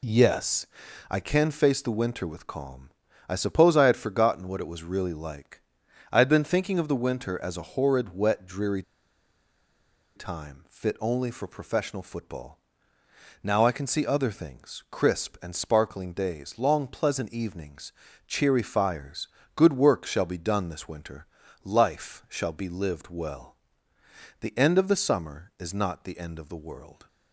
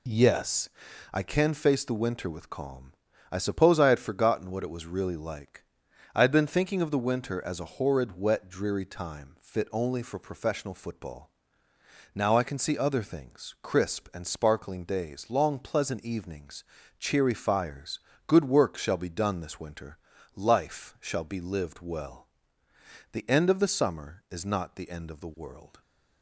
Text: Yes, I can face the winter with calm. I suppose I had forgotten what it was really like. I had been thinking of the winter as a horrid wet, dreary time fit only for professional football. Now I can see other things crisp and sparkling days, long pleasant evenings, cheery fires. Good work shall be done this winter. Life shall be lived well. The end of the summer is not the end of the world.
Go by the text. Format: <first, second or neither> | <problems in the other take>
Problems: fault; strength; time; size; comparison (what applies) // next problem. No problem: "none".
second | pauses between "dreary" and "time"; strong; at 8.8 s; 1.3 s long